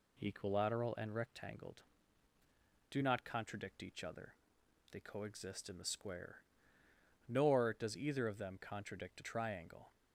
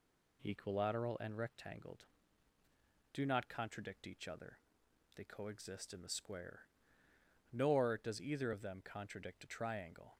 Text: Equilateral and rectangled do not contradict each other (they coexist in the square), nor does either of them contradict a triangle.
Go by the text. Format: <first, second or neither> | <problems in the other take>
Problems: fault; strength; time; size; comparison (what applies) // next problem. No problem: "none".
neither | none